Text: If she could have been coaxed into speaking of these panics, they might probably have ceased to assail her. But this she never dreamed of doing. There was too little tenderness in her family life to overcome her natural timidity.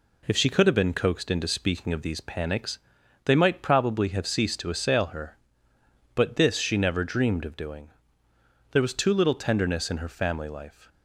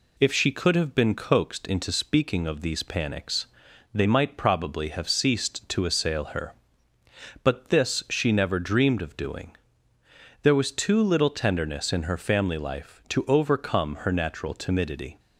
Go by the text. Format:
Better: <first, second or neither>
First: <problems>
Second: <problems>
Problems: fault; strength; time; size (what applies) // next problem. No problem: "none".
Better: second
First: stops before "to overcome her natural timidity"; at 10.8 s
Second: none